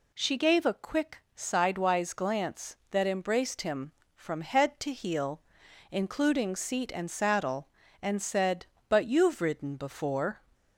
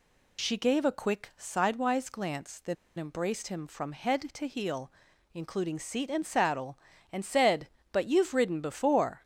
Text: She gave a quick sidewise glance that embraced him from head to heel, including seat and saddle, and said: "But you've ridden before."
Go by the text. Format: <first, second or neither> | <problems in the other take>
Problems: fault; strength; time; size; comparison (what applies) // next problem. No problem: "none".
first | pauses between "that" and "embraced"; slight; at 2.7 s; 0.23 s long